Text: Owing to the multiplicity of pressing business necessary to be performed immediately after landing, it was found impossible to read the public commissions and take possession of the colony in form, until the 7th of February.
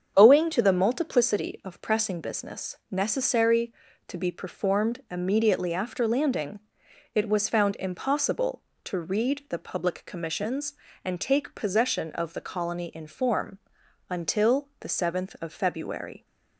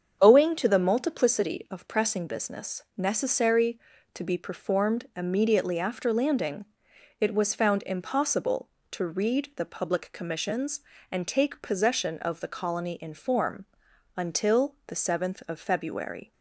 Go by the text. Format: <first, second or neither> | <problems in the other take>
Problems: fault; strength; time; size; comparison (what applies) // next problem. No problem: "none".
neither | starts louder than the rest; strong; the same in both